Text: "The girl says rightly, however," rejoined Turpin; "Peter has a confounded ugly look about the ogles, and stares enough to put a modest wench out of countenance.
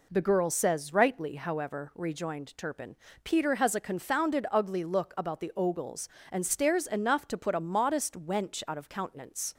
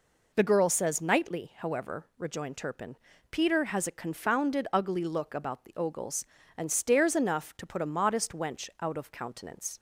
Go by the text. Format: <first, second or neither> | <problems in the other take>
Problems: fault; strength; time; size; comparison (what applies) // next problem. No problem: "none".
first | says "nightly" for "rightly"; at 1.0 s